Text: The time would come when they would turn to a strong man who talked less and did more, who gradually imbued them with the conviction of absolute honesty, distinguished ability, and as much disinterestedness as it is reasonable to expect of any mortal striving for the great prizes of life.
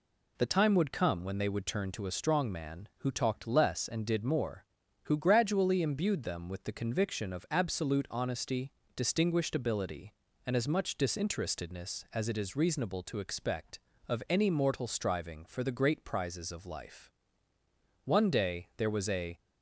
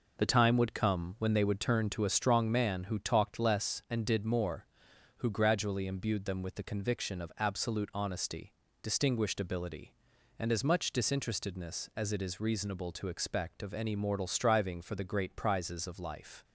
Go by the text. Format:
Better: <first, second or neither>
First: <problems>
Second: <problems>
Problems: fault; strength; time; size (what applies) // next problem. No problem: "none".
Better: second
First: goes on to say "One day there was a"; from 18.0 s on; 1.3 s long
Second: none